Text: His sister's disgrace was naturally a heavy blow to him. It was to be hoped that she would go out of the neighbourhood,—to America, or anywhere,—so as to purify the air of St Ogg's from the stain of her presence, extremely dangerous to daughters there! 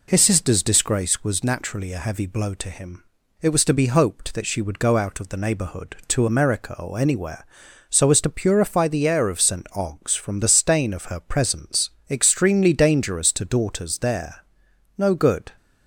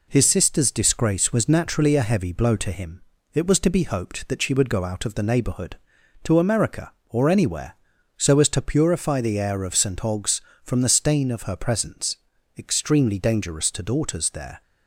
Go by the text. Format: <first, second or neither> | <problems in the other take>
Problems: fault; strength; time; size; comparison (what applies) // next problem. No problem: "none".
second | goes on to say "No good"; from 14.9 s on; 0.54 s long